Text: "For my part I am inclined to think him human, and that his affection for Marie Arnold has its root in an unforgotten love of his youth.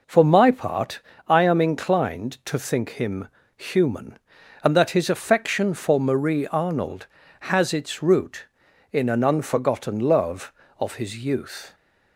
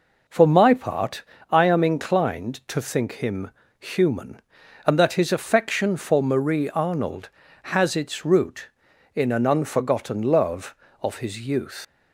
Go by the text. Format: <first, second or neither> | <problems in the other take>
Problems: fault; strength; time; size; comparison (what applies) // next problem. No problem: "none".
first | pauses between "part" and "I"; slight; at 1.2 s; 0.28 s long; slight in the first // pauses between "him" and "human"; slight; at 3.5 s; 0.28 s long; slight in the first // leaves "youth" unfinished; at 11.8 s; 120 ms